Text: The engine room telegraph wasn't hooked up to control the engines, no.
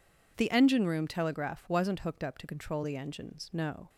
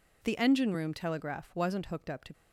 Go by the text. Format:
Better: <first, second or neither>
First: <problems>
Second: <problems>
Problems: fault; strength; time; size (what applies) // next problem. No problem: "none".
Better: first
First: none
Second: stops before "control the engines no"; at 2.3 s